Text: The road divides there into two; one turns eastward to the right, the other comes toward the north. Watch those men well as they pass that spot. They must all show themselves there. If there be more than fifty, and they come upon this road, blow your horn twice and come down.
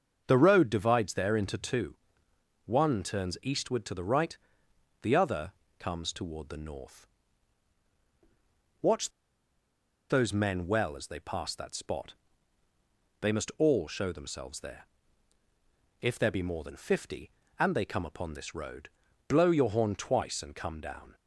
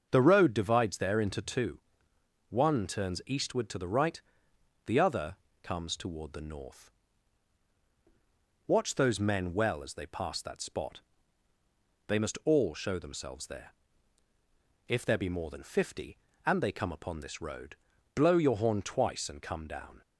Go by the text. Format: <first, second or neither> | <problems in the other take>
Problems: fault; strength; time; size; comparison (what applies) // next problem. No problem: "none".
second | starts louder than the rest; until 1.2 s; 6.5 dB; also in the second // pauses between "other" and "comes"; slight; at 5.5 s; 0.26 s long; slight in the second // pauses between "Watch" and "those"; at 9.0 s; 0.99 s long